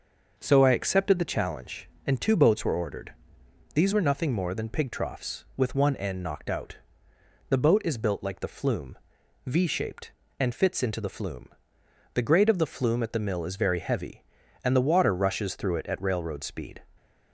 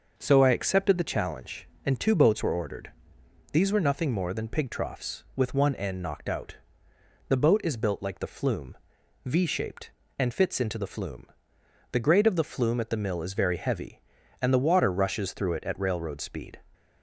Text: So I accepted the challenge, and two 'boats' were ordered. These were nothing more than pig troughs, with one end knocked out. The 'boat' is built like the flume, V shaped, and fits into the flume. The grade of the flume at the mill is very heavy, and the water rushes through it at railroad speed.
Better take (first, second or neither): neither